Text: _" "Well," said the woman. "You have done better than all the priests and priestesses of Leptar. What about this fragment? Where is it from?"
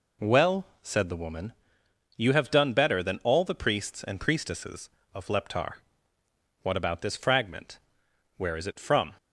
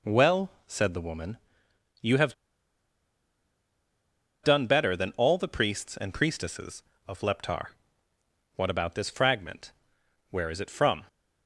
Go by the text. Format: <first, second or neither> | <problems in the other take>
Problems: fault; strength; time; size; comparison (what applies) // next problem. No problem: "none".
first | pauses between "have" and "done"; strong; at 2.3 s; 2.0 s long